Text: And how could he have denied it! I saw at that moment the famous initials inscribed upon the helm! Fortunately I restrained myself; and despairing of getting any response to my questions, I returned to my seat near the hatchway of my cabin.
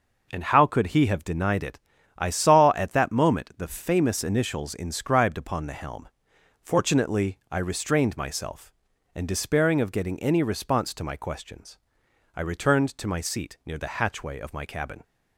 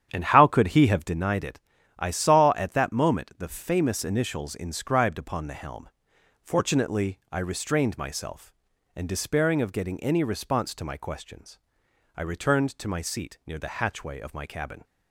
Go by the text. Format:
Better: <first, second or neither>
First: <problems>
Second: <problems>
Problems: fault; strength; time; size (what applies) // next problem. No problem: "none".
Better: first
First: none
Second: starts louder than the rest; strong; until 1.2 s; 9.5 dB